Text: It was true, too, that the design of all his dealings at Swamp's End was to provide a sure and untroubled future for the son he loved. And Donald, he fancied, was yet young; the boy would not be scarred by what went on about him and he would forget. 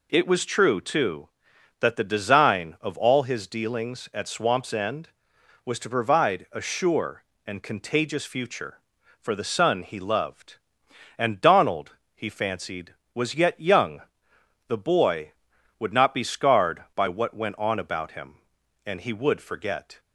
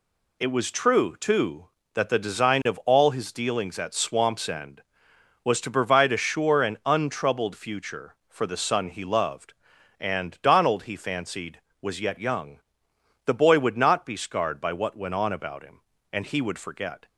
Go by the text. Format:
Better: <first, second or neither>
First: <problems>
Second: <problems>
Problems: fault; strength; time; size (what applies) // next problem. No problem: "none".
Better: second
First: says "contagious" for "untroubled"; at 7.6 s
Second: none